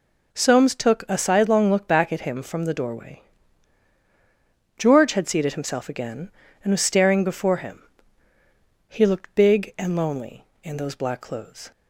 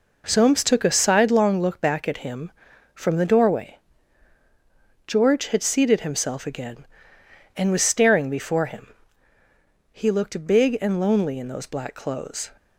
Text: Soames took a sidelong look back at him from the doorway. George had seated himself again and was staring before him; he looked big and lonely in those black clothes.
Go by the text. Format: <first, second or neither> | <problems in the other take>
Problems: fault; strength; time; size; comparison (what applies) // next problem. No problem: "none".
neither | none